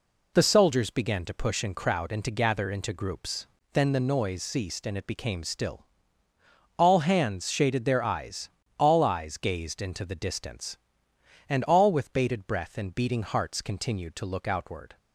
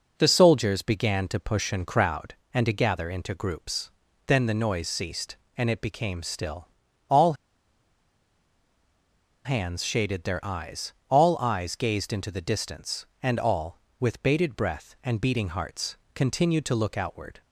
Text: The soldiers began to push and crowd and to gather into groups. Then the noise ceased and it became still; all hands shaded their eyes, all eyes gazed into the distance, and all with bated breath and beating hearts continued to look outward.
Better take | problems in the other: first | pauses between "all" and "hands"; strong; at 7.3 s; 2.1 s long // pauses between "hearts" and "continued"; slight; at 15.9 s; 0.18 s long

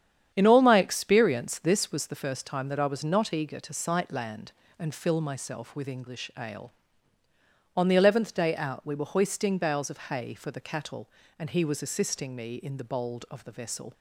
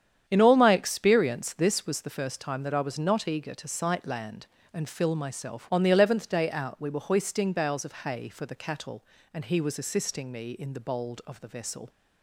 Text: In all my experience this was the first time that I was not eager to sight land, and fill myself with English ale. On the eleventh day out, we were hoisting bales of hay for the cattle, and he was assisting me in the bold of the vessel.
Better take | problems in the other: first | starts louder than the rest; strong; until 1.2 s; 9 dB; strong in the first // skips "with English ale"; at 5.7 s

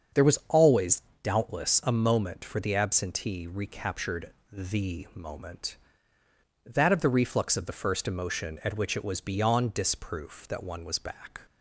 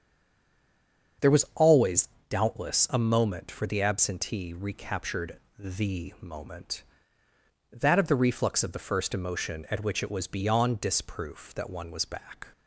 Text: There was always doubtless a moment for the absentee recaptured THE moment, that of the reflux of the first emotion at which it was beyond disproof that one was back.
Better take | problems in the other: first | stays silent before the first word; noticeable; until 1.1 s; 1.1 s long // starts louder than the rest; until 2.5 s; 7 dB; also in the first // pauses between "always" and "doubtless"; slight; at 2.0 s; 0.22 s long; slight in the first // pauses between "recaptured" and "THE"; slight; at 5.3 s; 0.20 s long; slight in the first

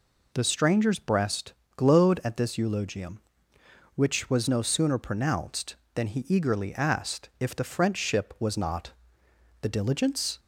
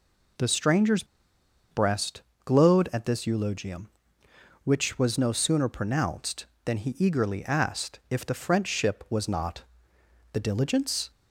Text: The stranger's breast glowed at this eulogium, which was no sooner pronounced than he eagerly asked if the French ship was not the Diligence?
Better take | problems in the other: first | pauses between "stranger's" and "breast"; noticeable; at 1.0 s; 0.67 s long // pauses between "breast" and "glowed"; slight; at 2.2 s; 0.22 s long; slight in the first // pauses between "not" and "the"; noticeable; at 9.6 s; 0.70 s long; noticeable in the first

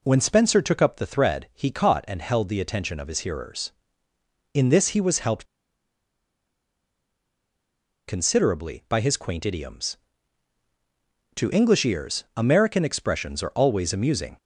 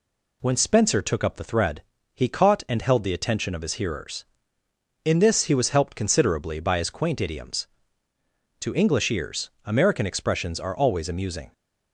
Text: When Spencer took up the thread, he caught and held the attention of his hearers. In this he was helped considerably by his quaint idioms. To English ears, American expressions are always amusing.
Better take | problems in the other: second | pauses between "helped" and "considerably"; strong; at 5.4 s; 2.6 s long

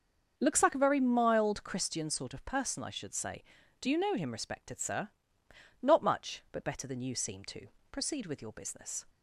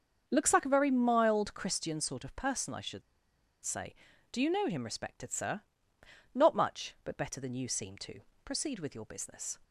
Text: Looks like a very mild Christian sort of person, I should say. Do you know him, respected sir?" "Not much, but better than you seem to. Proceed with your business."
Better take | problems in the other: first | starts louder than the rest; until 1.2 s; 6.5 dB; also in the first // pauses between "should" and "say"; noticeable; at 3.0 s; 0.63 s long

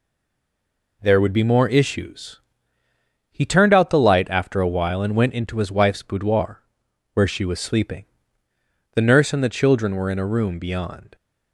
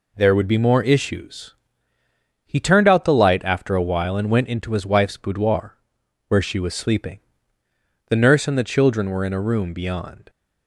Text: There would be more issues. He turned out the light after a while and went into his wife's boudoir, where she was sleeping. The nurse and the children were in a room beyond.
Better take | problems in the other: second | stays silent before the first word; until 1.0 s; 1.0 s long

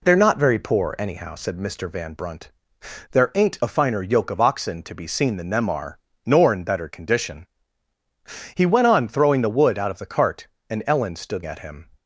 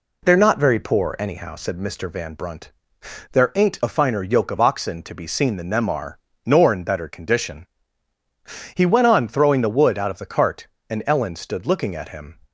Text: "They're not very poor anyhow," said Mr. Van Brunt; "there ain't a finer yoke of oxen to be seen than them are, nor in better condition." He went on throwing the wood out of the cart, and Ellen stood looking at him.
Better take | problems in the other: second | skips "looking"; at 11.4 s

